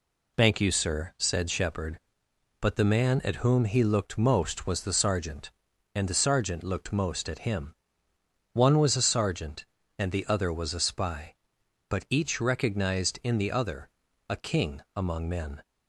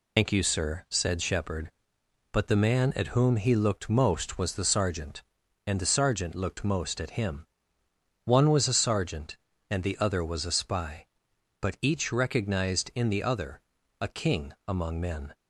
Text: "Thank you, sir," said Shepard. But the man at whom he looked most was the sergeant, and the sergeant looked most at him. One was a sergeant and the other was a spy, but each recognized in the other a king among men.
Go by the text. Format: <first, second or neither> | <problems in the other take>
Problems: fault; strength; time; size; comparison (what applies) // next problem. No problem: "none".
first | loses the start of "Thank"; at 0.1 s; 90 ms // pauses between "other" and "a"; at 13.6 s; 0.38 s long; also in the first